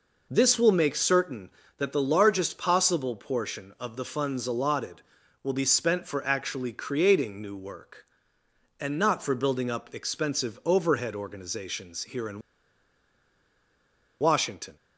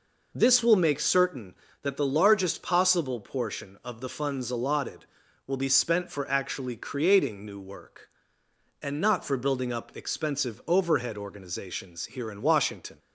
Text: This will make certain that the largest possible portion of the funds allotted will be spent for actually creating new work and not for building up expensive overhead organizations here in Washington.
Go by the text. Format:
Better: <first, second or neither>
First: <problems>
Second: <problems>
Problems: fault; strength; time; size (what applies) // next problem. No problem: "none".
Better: second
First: pauses between "in" and "Washington"; strong; at 12.4 s; 1.8 s long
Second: none